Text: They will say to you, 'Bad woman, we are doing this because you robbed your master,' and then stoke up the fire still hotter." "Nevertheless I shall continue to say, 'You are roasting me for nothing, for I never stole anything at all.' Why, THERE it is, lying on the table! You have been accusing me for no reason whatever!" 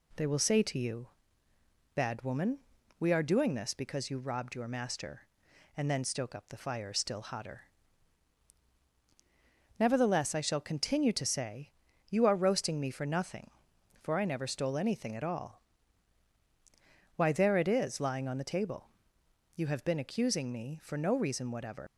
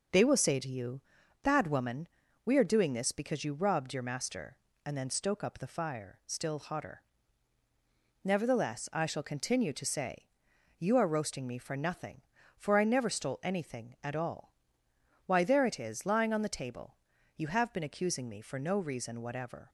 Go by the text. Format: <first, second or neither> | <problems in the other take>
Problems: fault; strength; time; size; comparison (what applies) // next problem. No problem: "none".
second | leaves "whatever" unfinished; at 21.8 s; 150 ms